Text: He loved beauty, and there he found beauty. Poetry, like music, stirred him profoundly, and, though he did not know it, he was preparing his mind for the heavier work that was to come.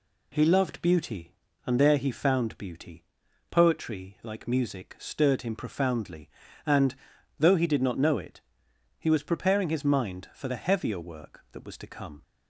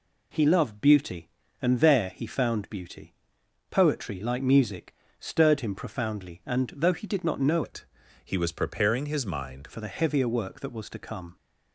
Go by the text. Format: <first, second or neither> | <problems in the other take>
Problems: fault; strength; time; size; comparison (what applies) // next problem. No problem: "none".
first | changes voice from "it" to "mind"; from 7.6 to 9.6 s; 2.0 s long